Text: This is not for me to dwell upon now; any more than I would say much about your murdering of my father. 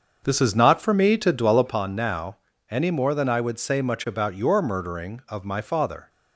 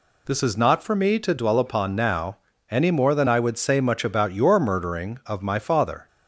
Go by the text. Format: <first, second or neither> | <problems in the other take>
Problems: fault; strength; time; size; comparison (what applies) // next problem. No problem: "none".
second | starts louder than the rest; until 1.9 s; 6.5 dB